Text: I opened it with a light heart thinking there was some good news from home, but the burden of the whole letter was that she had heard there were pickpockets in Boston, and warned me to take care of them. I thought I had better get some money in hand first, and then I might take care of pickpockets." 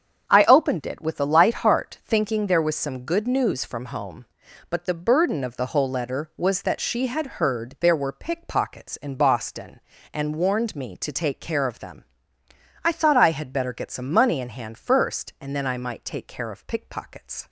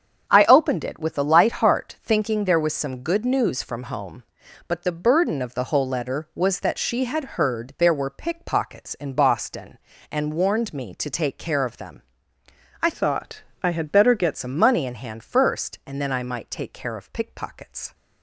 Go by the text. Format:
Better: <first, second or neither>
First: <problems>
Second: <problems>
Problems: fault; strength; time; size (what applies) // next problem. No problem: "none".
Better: first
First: starts louder than the rest; strong; until 1.3 s; 8 dB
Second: starts louder than the rest; strong; until 1.3 s; 8 dB // changes voice from "thought" to "get"; from 12.9 to 14.3 s; 1.4 s long // pauses between "thought" and "I"; slight; at 13.4 s; 0.20 s long